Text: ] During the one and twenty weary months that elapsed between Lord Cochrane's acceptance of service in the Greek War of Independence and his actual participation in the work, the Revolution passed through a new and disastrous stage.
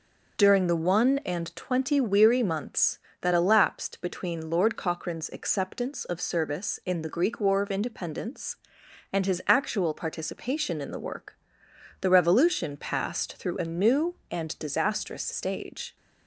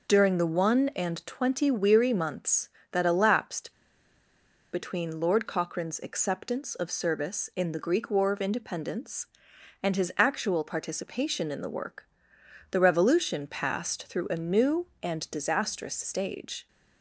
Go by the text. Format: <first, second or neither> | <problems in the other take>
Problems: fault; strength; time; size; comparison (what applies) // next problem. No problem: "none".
first | pauses between "elapsed" and "between"; at 3.7 s; 1.0 s long